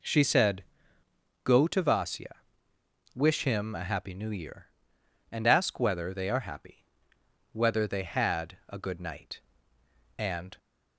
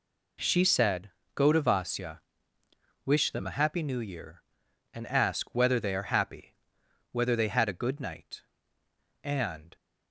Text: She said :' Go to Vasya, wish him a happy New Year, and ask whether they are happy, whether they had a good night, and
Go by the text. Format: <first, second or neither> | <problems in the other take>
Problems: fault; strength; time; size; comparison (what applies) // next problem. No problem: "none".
first | says "them" for "him"; at 3.3 s